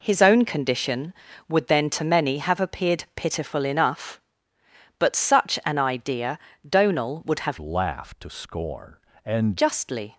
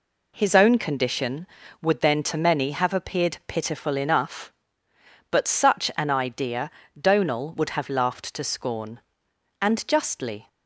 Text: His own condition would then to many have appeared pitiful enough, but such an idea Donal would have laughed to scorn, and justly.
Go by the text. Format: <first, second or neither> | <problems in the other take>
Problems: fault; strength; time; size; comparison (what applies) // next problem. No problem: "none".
second | pauses between "idea" and "Donal"; slight; at 6.3 s; 0.28 s long; slight in the second // changes voice from "laughed" to "and"; from 7.5 to 9.5 s; 2.0 s long